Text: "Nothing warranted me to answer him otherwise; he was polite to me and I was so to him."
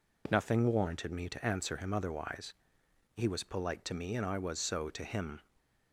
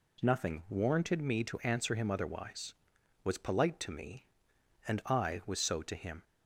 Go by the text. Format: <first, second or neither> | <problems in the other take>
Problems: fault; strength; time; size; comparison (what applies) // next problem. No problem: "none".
first | skips "he"; at 2.9 s